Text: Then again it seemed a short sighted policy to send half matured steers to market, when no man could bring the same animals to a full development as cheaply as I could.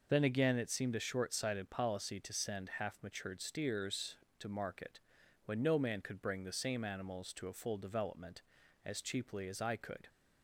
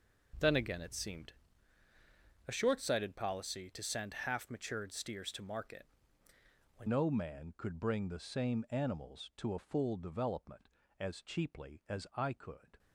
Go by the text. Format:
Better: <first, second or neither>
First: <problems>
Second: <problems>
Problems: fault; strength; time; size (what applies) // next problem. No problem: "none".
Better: first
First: none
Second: pauses between "seemed" and "a"; at 1.3 s; 1.1 s long // changes voice at "no"; from 6.8 s on; 5.9 s long